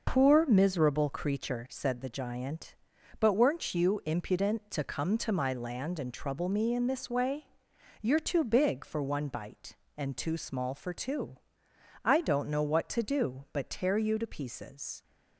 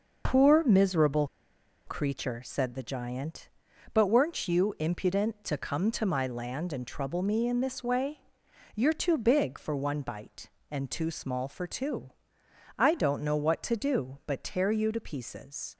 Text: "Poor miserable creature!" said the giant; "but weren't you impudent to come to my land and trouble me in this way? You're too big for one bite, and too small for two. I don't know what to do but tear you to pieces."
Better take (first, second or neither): first